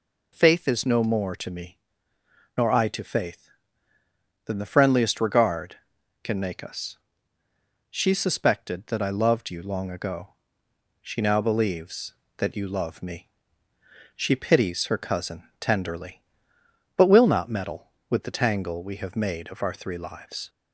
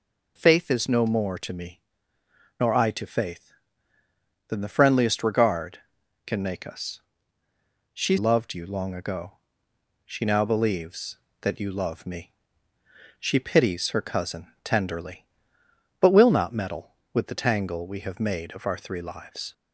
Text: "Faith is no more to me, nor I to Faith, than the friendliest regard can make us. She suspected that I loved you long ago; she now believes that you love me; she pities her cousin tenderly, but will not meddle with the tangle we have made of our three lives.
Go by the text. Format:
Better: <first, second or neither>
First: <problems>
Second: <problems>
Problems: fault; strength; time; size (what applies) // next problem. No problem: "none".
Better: first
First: none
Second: skips "suspected that I"; at 8.1 s